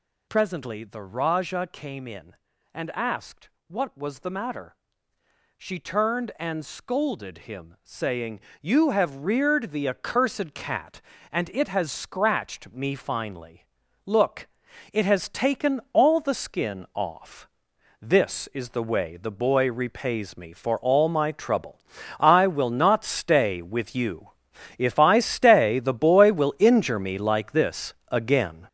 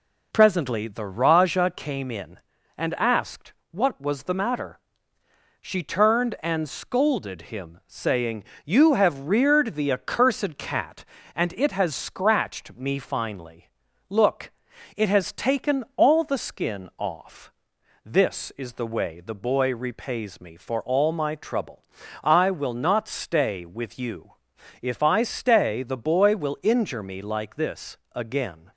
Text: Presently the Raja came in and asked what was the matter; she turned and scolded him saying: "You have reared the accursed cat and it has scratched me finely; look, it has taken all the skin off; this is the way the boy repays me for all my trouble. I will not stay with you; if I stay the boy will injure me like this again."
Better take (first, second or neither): second